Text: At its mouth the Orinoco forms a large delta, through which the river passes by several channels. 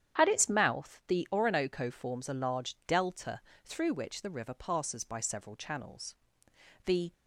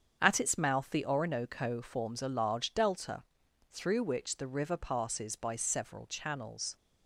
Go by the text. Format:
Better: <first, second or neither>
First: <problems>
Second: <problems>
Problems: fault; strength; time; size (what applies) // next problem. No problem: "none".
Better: second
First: starts louder than the rest; strong; until 1.2 s; 9 dB // goes on to say "The"; slight; from 6.8 s on; 0.26 s long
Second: starts louder than the rest; strong; until 1.2 s; 7.5 dB